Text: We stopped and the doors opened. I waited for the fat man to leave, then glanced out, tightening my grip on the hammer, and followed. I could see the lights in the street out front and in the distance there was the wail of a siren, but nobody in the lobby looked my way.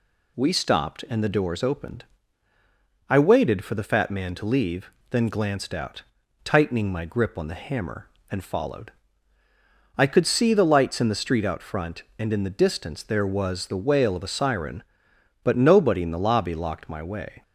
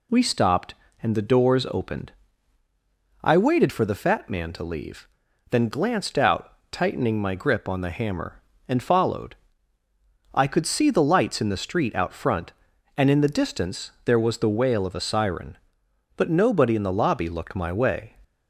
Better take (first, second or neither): second